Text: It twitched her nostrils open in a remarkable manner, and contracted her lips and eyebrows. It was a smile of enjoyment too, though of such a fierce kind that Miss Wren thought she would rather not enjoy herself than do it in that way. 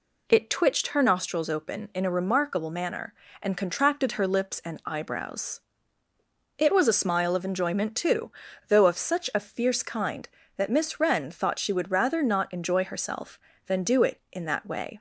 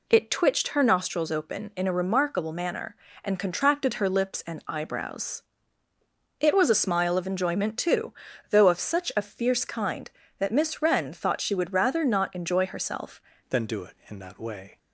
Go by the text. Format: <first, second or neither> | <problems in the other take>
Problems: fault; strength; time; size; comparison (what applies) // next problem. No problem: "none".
first | changes voice at "than"; from 13.4 s on; 1.3 s long